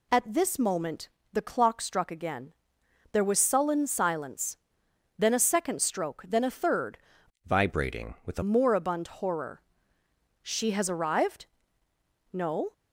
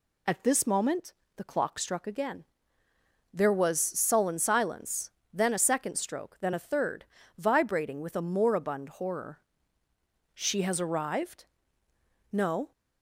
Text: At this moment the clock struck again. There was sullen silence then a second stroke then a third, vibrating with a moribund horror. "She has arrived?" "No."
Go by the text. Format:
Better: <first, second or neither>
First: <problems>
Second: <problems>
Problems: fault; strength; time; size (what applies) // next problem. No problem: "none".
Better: second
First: pauses between "moment" and "the"; slight; at 1.0 s; 0.24 s long // pauses between "silence" and "then"; noticeable; at 4.5 s; 0.62 s long // changes voice from "vibrating" to "a"; from 7.4 to 8.4 s; 1.0 s long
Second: pauses between "moment" and "the"; slight; at 1.1 s; 0.24 s long // pauses between "silence" and "then"; slight; at 5.0 s; 0.24 s long